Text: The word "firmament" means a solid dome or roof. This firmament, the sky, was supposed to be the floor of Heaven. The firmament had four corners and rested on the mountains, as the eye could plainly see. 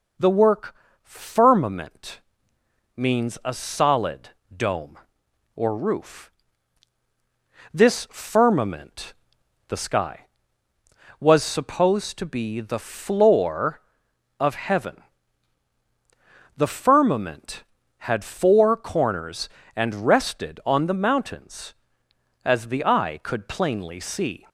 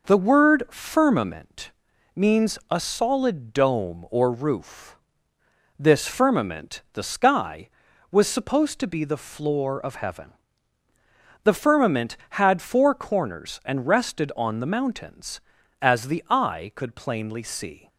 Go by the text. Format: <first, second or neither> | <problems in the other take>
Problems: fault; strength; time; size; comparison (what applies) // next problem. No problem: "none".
second | says "work" for "word"; at 0.3 s // pauses between "firmament" and "means"; noticeable; at 2.2 s; 0.76 s long; also in the second // pauses between "solid" and "dome"; slight; at 4.3 s; 0.24 s long